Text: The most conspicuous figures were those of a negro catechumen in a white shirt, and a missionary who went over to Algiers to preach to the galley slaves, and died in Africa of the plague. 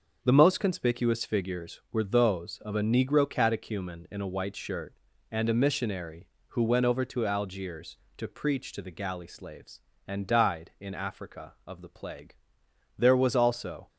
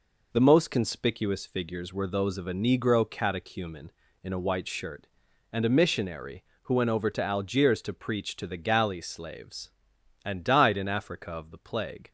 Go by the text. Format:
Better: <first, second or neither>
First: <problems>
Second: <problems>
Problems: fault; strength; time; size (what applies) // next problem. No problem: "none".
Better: second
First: goes on to say "There was also"; noticeable; from 12.9 s on; 0.90 s long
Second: none